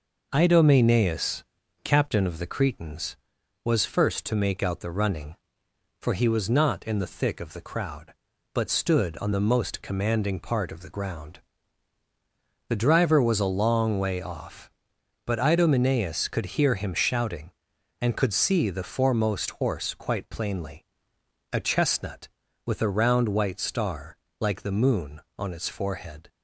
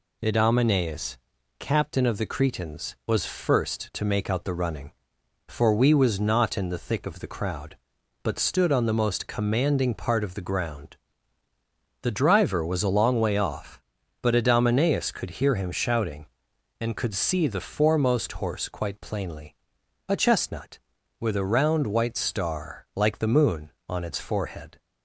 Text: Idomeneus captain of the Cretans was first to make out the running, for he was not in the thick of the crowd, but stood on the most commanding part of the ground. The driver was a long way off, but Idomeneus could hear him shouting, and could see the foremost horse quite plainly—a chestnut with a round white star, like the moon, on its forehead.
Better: first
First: pauses between "Idomeneus" and "captain"; at 1.4 s; 0.40 s long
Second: pauses between "Idomeneus" and "captain"; at 1.1 s; 0.42 s long // says "we" for "he"; at 5.7 s

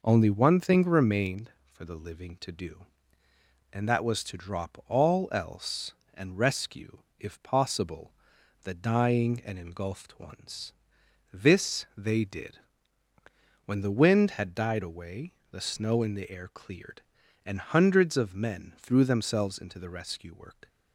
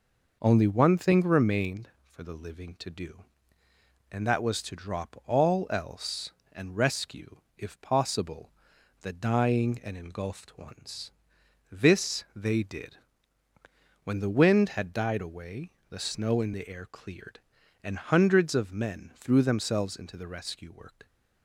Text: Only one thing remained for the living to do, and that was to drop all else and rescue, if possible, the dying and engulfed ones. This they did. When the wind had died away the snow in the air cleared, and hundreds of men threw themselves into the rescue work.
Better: neither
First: pauses between "away" and "the"; slight; at 15.3 s; 0.20 s long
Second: pauses between "away" and "the"; slight; at 15.7 s; 0.20 s long

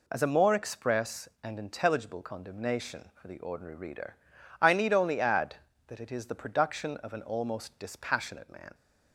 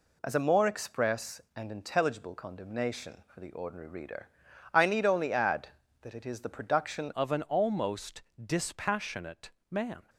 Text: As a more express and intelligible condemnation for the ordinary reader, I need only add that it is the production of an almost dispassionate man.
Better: first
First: none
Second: changes voice at "of"; from 7.1 s on; 2.9 s long // pauses between "almost" and "dispassionate"; slight; at 8.2 s; 0.22 s long // pauses between "dispassionate" and "man"; slight; at 9.5 s; 0.20 s long

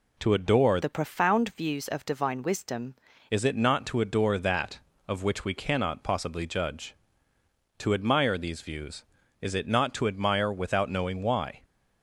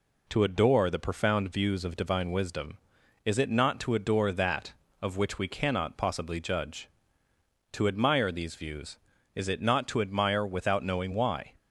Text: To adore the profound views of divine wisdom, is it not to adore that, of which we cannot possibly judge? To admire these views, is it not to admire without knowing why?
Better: second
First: changes voice from "the" to "wisdom"; from 0.8 to 2.9 s; 2.1 s long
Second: none

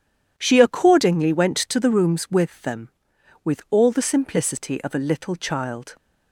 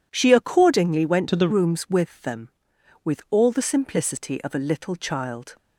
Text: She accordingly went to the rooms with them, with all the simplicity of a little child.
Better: first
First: none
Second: changes voice from "to" to "the"; from 1.2 to 1.4 s; 0.2 s long

